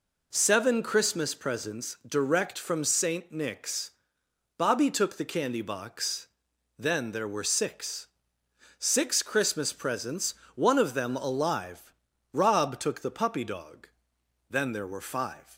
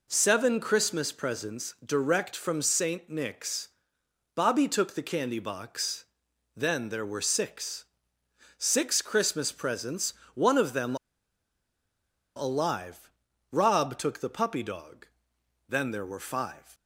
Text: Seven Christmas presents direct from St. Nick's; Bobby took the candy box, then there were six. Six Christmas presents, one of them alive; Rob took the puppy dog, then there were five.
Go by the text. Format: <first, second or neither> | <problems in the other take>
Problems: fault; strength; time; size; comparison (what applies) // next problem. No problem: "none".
first | pauses between "them" and "alive"; strong; at 10.9 s; 1.4 s long